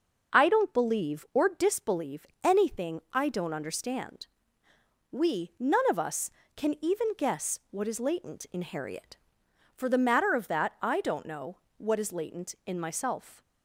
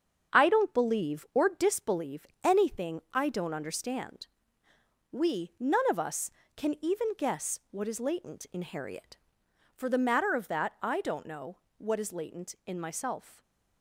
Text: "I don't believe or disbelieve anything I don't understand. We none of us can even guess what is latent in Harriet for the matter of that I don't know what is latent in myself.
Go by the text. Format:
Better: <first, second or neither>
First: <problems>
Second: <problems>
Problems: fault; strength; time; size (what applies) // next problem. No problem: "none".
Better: first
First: pauses between "disbelieve" and "anything"; slight; at 2.2 s; 0.18 s long // pauses between "know" and "what"; slight; at 11.5 s; 0.20 s long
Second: gets quieter; noticeable; throughout; 6 dB // pauses between "disbelieve" and "anything"; slight; at 2.2 s; 0.18 s long // pauses between "know" and "what"; slight; at 11.5 s; 0.20 s long